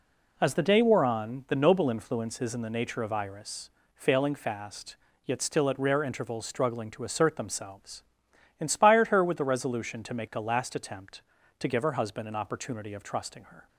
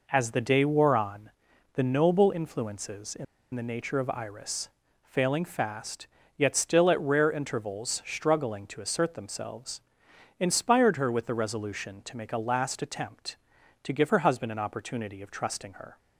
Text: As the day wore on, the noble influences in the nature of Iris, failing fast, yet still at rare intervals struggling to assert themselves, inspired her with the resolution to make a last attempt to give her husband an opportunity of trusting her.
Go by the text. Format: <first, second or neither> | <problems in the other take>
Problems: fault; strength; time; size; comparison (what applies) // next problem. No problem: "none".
first | pauses between "in" and "the"; slight; at 3.2 s; 0.28 s long